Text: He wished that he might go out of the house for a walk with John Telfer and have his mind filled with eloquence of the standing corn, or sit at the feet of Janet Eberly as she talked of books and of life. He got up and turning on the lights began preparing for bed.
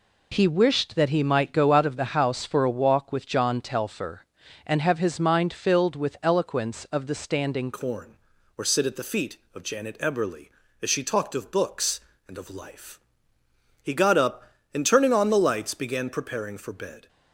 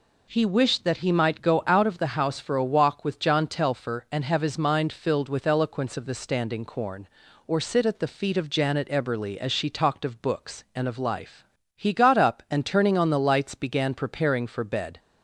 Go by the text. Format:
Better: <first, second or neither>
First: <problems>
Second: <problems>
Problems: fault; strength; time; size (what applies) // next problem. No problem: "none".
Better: second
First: changes voice at "corn"; from 7.7 s on; 9.3 s long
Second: none